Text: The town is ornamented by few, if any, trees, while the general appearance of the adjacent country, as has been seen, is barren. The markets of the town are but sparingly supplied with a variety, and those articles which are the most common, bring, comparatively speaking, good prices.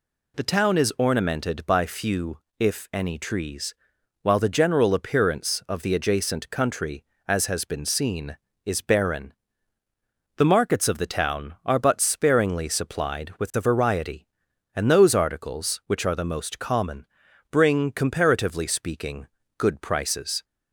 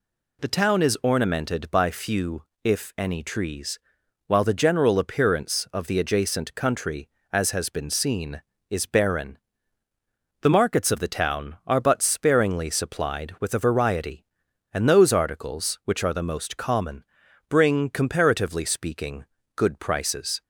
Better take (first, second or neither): neither